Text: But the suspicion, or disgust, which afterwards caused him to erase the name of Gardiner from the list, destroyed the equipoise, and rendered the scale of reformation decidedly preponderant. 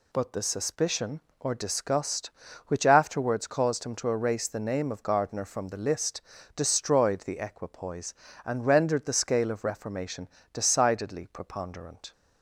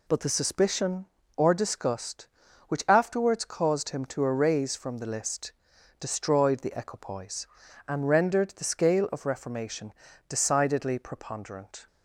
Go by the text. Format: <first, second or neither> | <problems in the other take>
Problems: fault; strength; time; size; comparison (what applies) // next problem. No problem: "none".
first | skips "the name of Gardiner"; at 4.7 s // pauses between "reformation" and "decidedly"; slight; at 9.9 s; 0.36 s long; slight in the first